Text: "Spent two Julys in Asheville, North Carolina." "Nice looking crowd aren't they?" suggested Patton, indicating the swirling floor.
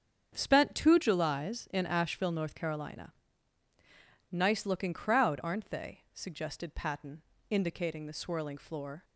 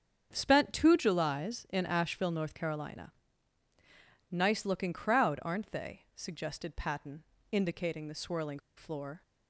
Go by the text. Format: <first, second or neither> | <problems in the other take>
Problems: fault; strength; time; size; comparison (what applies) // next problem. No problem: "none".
first | starts louder than the rest; strong; until 1.3 s; 7.5 dB; strong in the first // pauses between "swirling" and "floor"; slight; at 8.5 s; 0.17 s long